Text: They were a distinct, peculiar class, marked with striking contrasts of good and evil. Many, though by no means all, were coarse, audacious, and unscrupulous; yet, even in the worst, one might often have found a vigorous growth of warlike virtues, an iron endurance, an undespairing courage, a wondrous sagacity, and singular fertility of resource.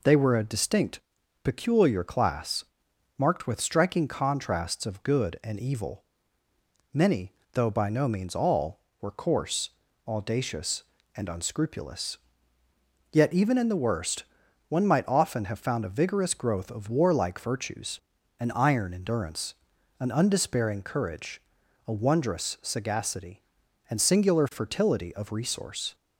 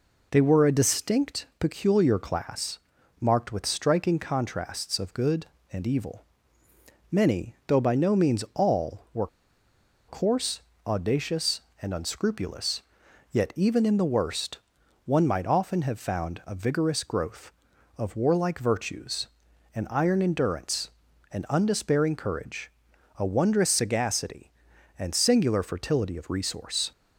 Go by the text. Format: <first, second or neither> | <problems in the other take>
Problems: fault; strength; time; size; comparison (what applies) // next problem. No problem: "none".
first | pauses between "were" and "coarse"; noticeable; at 9.2 s; 0.80 s long